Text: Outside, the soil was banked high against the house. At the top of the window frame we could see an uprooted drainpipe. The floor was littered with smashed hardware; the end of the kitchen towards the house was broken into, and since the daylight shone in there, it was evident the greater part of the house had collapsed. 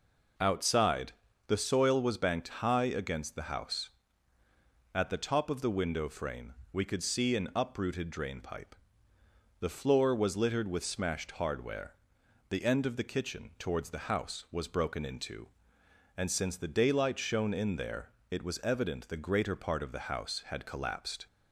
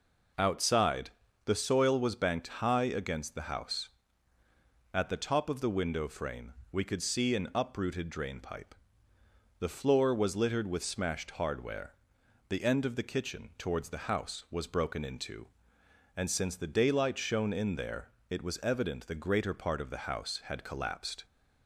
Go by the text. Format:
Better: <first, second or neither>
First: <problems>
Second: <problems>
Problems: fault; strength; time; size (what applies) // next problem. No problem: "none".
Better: neither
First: pauses between "frame" and "we"; slight; at 6.5 s; 0.18 s long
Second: pauses between "frame" and "we"; slight; at 6.5 s; 0.18 s long